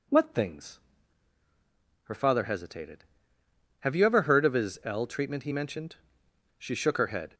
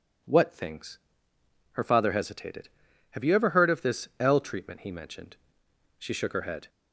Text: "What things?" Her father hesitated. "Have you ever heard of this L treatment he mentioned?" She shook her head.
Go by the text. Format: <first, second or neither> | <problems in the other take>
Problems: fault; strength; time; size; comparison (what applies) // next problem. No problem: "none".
second | says "his" for "this"; at 4.5 s